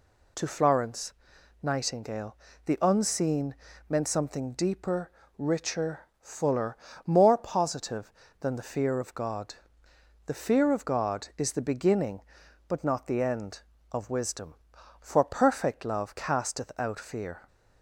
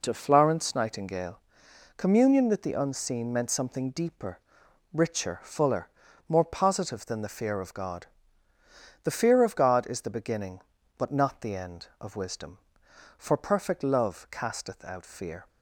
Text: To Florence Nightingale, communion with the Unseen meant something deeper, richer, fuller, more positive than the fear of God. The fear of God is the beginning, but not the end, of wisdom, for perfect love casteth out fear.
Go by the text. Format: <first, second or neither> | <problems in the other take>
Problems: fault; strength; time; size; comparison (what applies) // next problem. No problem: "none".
second | pauses between "Florence" and "Nightingale"; noticeable; at 1.1 s; 0.50 s long // skips "communion with"; at 2.5 s // pauses between "Unseen" and "meant"; slight; at 3.5 s; 0.34 s long